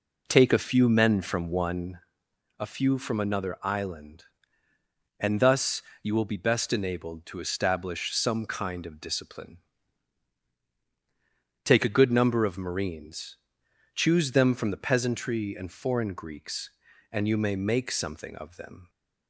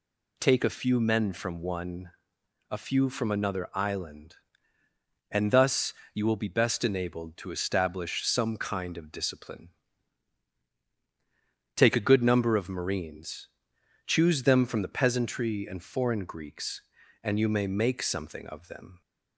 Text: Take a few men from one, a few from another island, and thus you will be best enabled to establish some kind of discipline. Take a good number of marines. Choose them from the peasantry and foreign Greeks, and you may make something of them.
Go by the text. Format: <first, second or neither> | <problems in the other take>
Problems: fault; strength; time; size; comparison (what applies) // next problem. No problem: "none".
second | starts louder than the rest; noticeable; until 2.0 s; 4 dB // pauses between "thus" and "you"; slight; at 5.8 s; 0.20 s long; slight in the second